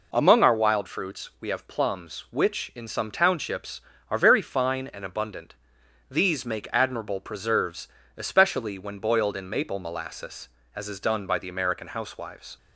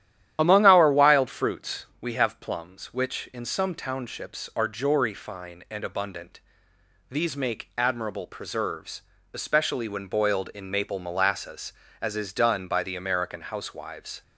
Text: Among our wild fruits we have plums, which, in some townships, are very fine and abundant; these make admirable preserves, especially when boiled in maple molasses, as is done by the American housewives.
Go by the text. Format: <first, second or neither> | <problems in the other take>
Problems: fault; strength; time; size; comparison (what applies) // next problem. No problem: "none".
first | starts louder than the rest; strong; until 1.4 s; 11.5 dB // pauses between "fruits" and "we"; slight; at 1.8 s; 0.16 s long // says "jory" for "very"; at 4.6 s